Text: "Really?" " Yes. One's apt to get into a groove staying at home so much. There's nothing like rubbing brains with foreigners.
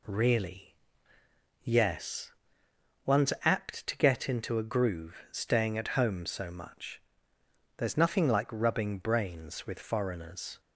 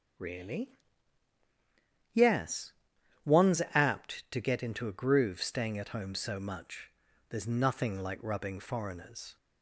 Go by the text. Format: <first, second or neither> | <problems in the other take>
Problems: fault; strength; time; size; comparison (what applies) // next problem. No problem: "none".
first | skips "brains with"; at 8.5 s